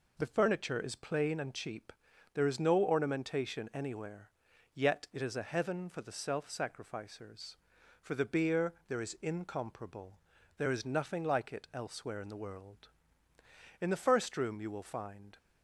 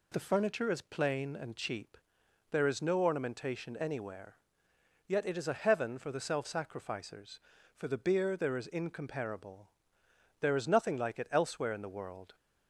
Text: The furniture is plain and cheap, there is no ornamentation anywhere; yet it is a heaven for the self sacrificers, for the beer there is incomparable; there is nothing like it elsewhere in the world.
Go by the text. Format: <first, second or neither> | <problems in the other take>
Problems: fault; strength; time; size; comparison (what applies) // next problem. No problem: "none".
second | goes on to say "In the first room you will find"; from 13.7 s on; 1.5 s long